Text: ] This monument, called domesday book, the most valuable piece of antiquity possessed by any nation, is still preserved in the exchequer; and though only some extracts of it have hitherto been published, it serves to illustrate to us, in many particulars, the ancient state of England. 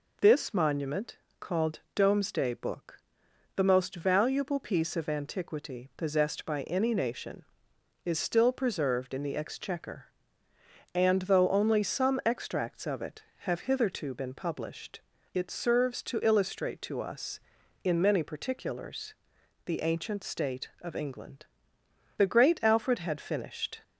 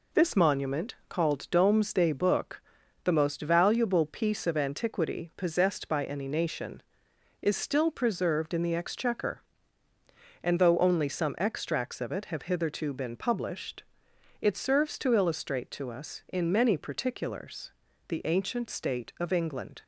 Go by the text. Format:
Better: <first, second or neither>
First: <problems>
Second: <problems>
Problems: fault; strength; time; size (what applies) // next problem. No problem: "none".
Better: second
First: goes on to say "The great Alfred had finished"; from 22.1 s on; 1.6 s long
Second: none